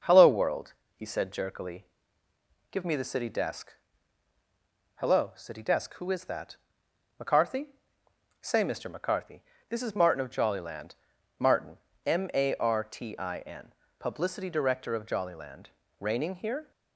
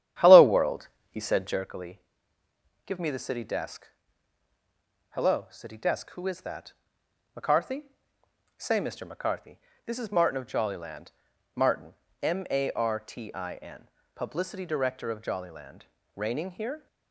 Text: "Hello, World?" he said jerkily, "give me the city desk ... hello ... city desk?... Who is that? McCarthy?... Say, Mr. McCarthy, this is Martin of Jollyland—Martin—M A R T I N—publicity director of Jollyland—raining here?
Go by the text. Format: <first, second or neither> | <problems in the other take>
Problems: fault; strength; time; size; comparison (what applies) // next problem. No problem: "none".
first | starts louder than the rest; strong; until 1.7 s; 10 dB